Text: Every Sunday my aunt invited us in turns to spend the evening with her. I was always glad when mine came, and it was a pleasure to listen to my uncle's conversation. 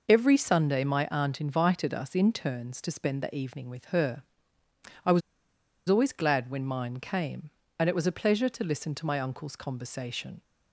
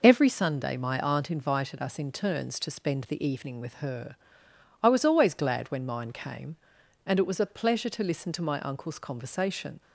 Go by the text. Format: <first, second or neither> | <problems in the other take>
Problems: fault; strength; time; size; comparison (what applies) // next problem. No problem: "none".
second | pauses between "was" and "always"; noticeable; at 5.2 s; 0.68 s long